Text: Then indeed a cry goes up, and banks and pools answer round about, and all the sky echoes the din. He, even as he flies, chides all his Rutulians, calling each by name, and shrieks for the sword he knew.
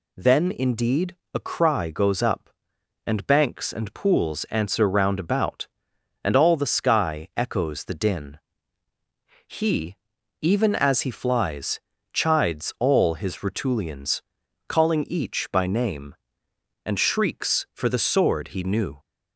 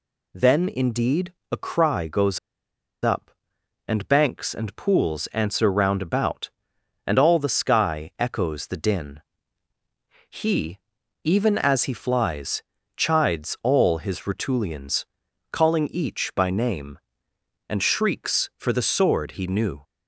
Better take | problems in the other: first | pauses between "indeed" and "a"; slight; at 1.3 s; 0.18 s long; slight in the first // pauses between "goes" and "up"; noticeable; at 2.3 s; 0.64 s long

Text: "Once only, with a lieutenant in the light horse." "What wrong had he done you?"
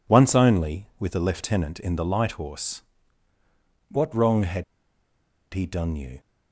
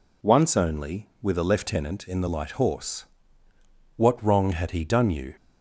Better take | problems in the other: second | pauses between "had" and "he"; noticeable; at 4.6 s; 0.89 s long

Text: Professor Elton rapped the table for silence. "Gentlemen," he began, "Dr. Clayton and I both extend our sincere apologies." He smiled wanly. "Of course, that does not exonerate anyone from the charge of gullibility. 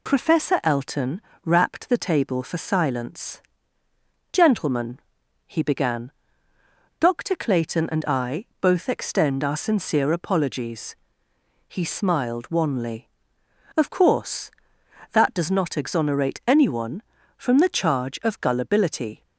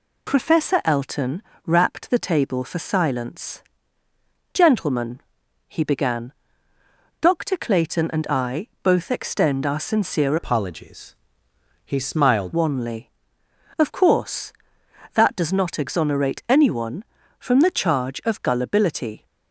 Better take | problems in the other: first | pauses between "Elton" and "rapped"; slight; at 1.4 s; 0.24 s long; slight in the first // changes voice from "apologies" to "smiled"; from 10.3 to 12.5 s; 2.2 s long

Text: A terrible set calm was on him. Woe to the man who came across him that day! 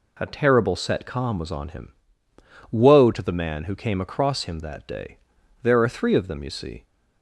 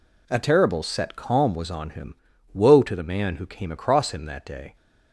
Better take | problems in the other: second | goes on to say "There are three of them you see"; noticeable; from 5.6 s on; 1.2 s long

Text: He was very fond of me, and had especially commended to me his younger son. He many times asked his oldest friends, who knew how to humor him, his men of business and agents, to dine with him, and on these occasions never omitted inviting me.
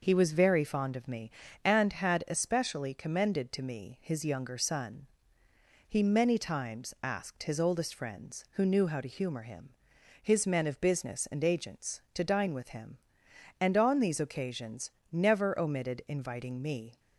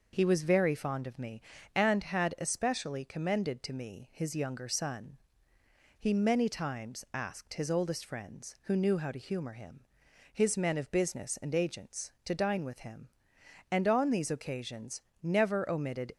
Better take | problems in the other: first | pauses between "occasions" and "never"; slight; at 15.0 s; 0.18 s long; slight in the first // stops before "inviting me"; at 16.1 s

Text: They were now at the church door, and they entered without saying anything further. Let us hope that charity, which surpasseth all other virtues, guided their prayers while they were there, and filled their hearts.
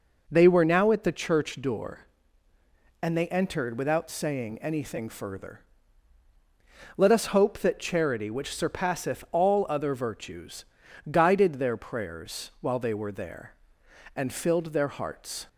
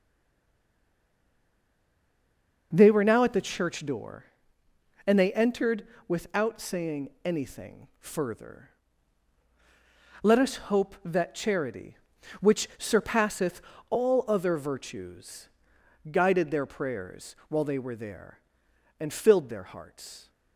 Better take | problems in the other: first | stays silent before the first word; strong; until 2.7 s; 2.7 s long // pauses between "entered" and "without"; slight; at 5.8 s; 0.22 s long // pauses between "surpasseth" and "all"; slight; at 13.5 s; 0.30 s long

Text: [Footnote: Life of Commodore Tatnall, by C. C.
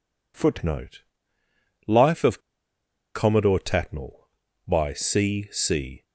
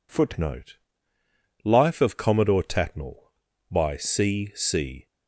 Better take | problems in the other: second | pauses between "of" and "Commodore"; noticeable; at 2.4 s; 0.73 s long

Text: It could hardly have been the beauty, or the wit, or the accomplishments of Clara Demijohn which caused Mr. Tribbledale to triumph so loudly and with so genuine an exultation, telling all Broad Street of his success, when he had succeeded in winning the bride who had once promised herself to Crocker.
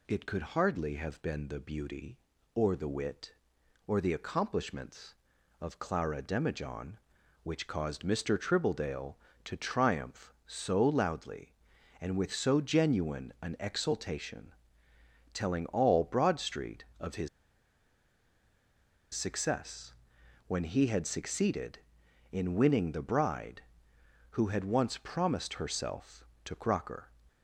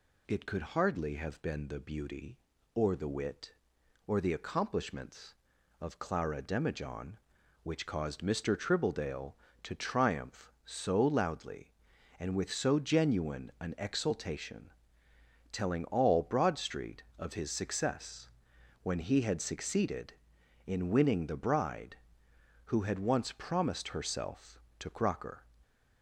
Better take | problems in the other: second | pauses between "his" and "success"; strong; at 17.2 s; 1.8 s long

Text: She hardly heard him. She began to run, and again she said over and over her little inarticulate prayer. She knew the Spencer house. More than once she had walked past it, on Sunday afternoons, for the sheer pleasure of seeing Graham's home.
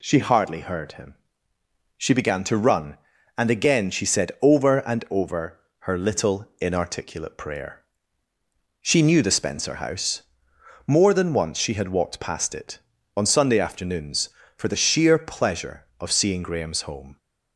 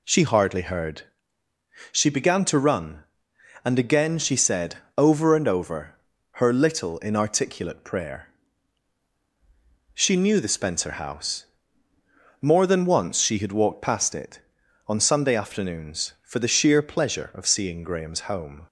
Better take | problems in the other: first | skips "him"; at 1.4 s // pauses between "said" and "over"; slight; at 4.7 s; 0.20 s long // pauses between "over" and "her"; at 5.9 s; 0.38 s long; slight in the first

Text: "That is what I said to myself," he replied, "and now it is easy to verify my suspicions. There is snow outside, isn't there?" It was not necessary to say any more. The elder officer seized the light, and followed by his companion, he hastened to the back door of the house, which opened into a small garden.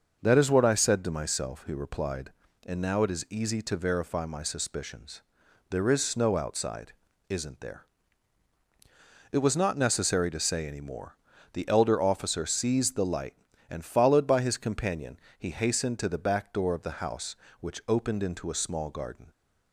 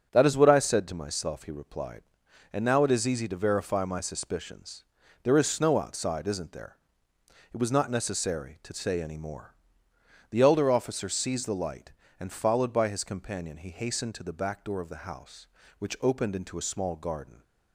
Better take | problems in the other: neither | starts louder than the rest; the same in both

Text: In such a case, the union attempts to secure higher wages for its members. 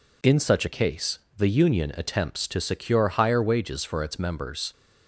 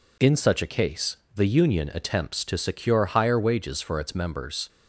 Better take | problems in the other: neither | none

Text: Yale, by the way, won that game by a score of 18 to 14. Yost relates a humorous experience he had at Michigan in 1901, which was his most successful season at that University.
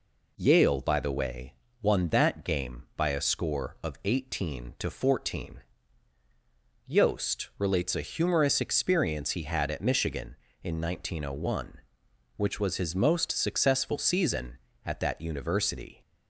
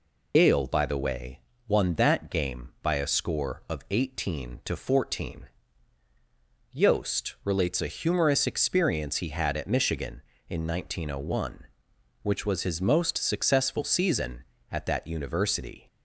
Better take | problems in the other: first | loses the start of "Yale"; at 0.3 s; 120 ms

